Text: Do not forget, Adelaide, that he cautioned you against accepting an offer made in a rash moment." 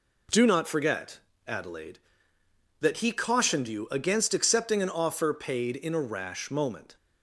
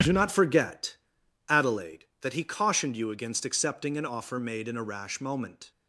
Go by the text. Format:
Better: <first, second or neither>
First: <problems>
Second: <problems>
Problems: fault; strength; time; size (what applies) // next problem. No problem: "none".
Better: second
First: says "paid" for "made"; at 5.3 s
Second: none